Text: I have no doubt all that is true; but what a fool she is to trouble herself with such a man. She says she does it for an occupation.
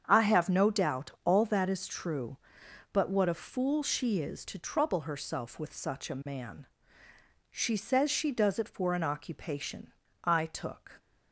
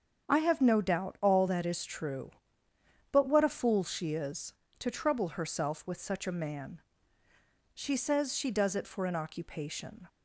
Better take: second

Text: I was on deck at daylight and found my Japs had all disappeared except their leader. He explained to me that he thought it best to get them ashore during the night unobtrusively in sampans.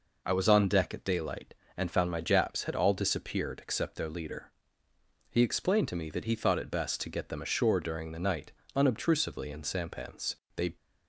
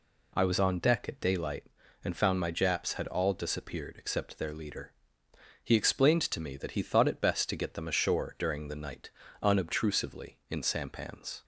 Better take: second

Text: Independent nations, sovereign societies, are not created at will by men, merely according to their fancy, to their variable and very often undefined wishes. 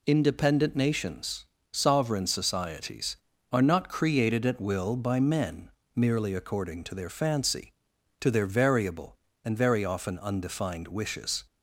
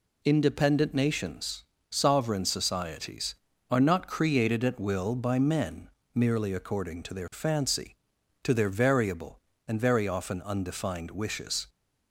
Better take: neither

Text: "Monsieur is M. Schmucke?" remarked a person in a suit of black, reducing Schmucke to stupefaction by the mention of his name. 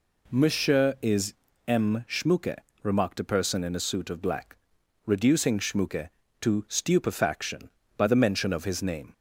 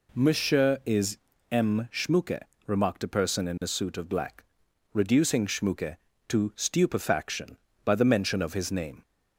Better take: neither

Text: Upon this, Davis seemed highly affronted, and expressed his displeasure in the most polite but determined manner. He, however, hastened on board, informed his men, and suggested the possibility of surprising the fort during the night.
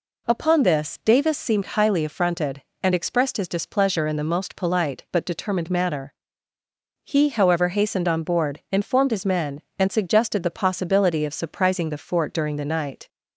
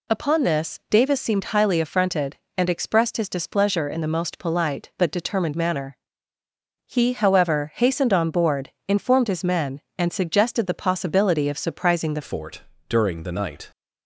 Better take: first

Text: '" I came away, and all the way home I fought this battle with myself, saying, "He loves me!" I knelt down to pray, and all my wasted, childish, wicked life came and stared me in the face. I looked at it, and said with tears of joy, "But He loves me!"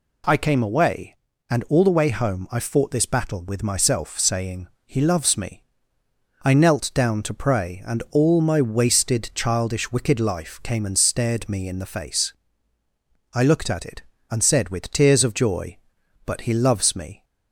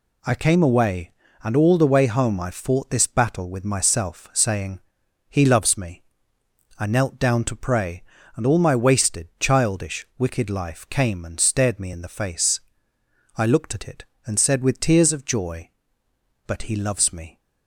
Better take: neither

